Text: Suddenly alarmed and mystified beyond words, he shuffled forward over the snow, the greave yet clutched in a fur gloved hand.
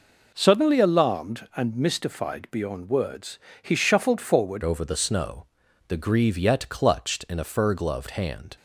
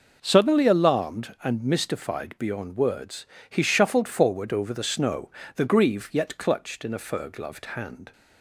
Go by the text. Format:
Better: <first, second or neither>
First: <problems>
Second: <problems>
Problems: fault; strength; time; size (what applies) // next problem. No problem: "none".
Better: second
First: changes voice at "over"; from 4.6 s on; 3.9 s long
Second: none